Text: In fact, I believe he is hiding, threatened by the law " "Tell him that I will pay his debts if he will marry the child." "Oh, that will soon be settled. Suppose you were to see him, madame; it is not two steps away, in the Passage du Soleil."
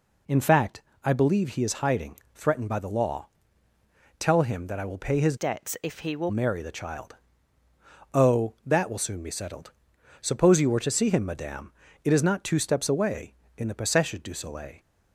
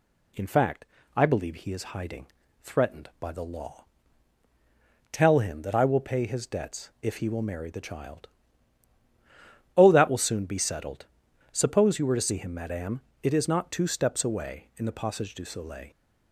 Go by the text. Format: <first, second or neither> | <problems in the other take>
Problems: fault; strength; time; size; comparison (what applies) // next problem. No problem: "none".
second | changes voice from "debts" to "will"; from 5.3 to 6.3 s; 1.0 s long